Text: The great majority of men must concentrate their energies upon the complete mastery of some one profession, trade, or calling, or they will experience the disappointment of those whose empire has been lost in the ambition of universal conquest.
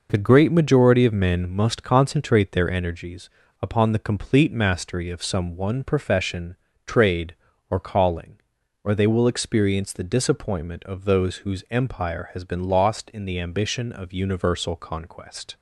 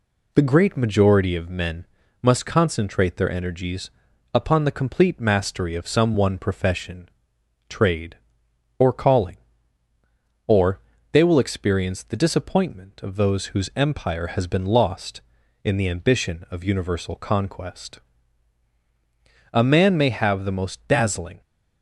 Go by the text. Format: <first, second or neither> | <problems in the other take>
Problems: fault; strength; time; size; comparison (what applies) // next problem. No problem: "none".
first | pauses between "men" and "must"; slight; at 1.8 s; 0.36 s long // pauses between "energies" and "upon"; at 3.8 s; 0.44 s long; slight in the first // pauses between "or" and "they"; slight; at 10.7 s; 0.32 s long // goes on to say "A man may have the most dazzling"; strong; from 19.5 s on; 1.8 s long